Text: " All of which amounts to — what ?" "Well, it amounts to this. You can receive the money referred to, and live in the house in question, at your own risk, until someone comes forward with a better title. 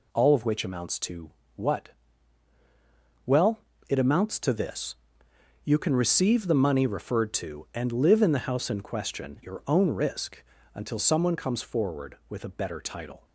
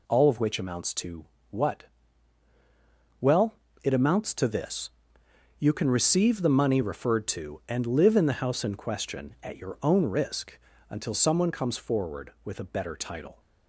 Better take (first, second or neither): second